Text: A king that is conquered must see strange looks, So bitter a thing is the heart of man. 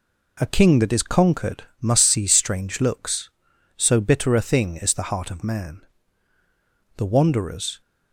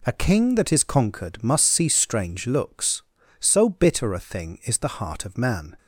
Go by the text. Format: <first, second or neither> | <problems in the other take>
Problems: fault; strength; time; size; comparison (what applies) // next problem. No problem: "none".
second | pauses between "conquered" and "must"; slight; at 1.6 s; 0.16 s long // goes on to say "The wanderers"; noticeable; from 6.9 s on; 0.84 s long